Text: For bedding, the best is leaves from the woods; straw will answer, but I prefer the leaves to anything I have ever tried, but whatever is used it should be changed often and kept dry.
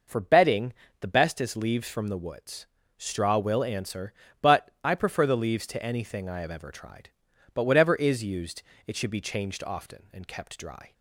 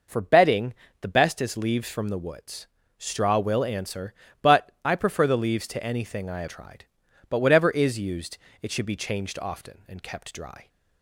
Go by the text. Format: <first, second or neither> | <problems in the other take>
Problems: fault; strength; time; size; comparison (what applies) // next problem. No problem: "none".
first | skips "ever"; at 6.4 s // pauses between "used" and "it"; slight; at 8.3 s; 0.24 s long; slight in the first